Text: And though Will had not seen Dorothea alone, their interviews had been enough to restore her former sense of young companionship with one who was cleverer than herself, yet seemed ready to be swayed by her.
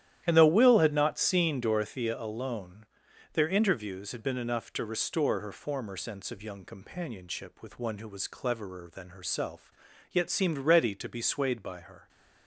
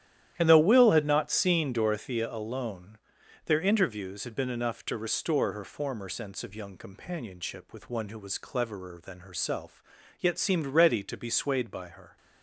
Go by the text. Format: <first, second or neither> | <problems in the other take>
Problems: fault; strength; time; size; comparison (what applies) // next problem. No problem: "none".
neither | starts louder than the rest; strong; the same in both